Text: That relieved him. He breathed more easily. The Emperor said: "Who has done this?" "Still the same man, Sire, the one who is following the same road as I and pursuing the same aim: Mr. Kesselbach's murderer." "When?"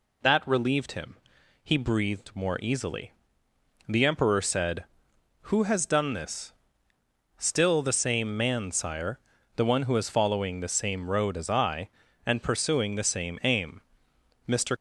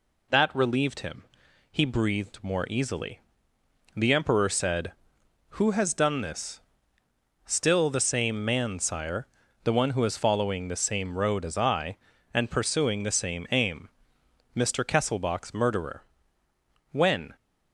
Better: second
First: stops before "Kesselbach's murderer When"; at 14.7 s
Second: none

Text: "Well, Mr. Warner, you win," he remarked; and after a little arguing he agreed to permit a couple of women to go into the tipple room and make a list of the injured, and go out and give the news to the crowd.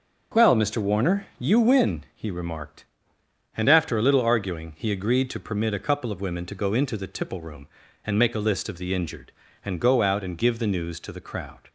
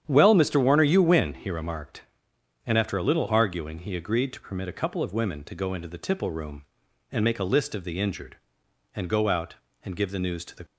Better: first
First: none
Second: starts louder than the rest; strong; until 1.0 s; 9.5 dB // stops before "crowd"; at 10.6 s

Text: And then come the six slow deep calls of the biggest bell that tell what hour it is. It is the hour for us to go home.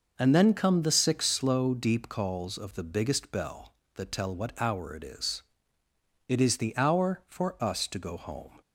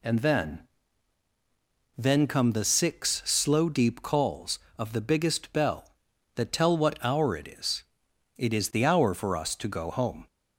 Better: first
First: none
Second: says "then" twice; at 1.9 s

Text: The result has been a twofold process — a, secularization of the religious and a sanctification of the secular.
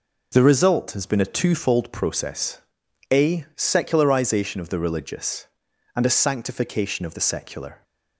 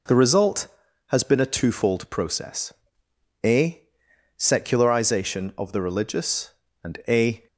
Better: first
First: none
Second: stops before "sanctification of the secular"; at 7.4 s

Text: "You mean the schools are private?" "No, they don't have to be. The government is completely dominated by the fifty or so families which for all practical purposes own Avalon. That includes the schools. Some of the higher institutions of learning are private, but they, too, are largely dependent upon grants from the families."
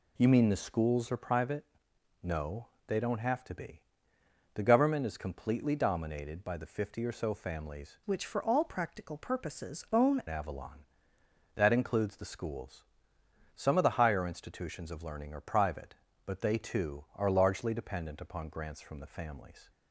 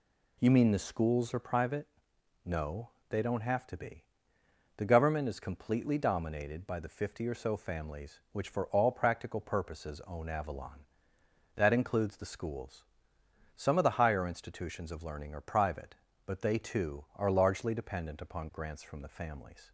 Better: second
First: changes voice from "which" to "own"; from 8.0 to 10.2 s; 2.2 s long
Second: none

